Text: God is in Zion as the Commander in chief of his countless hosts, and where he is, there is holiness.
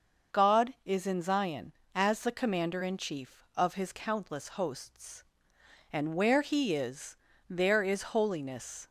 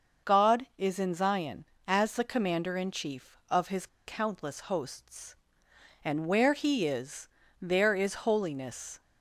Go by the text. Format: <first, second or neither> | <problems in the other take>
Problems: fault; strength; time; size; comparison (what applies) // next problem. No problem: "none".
first | starts louder than the rest; noticeable; until 1.3 s; 6 dB; noticeable in the first // pauses between "his" and "countless"; slight; at 3.8 s; 0.19 s long